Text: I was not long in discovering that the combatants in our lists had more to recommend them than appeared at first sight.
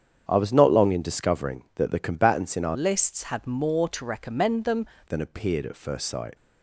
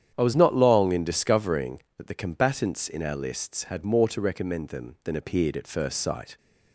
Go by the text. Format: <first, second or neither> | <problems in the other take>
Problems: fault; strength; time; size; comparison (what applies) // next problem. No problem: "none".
second | starts louder than the rest; strong; until 1.2 s; 8.5 dB; strong in the second // changes voice from "lists" to "them"; from 2.7 to 4.8 s; 2.1 s long